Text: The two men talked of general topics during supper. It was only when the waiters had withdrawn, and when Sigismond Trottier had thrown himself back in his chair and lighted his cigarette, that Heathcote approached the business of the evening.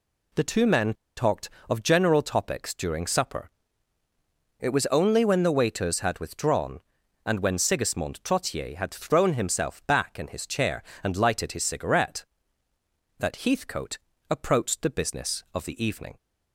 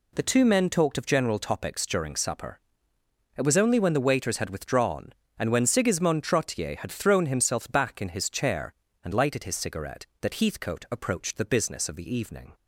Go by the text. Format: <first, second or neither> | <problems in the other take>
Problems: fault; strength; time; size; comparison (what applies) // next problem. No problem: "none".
second | pauses between "men" and "talked"; slight; at 0.9 s; 0.22 s long // pauses between "Heathcote" and "approached"; slight; at 13.9 s; 0.32 s long